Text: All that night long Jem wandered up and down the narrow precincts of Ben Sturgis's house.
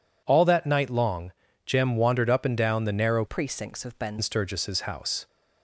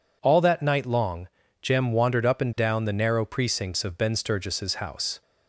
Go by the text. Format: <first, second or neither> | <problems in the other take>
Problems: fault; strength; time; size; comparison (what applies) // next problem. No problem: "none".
second | pauses between "long" and "Jem"; slight; at 1.3 s; 0.32 s long; slight in the second // changes voice from "precincts" to "Ben"; from 3.2 to 4.1 s; 0.9 s long